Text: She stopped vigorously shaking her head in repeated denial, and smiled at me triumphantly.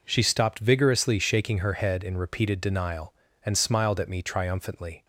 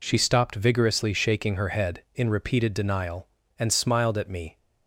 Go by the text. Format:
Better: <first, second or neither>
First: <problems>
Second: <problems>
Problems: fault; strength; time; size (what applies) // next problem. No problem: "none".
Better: first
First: none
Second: stops before "triumphantly"; at 4.5 s